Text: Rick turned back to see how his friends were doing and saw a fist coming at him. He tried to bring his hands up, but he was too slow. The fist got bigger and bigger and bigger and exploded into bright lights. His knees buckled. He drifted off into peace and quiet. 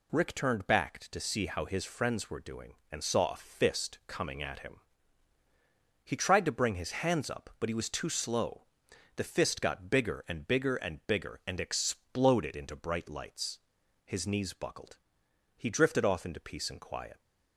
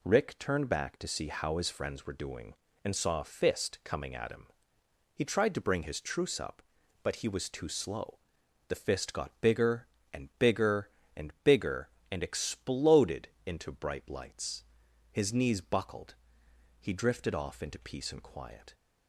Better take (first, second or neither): first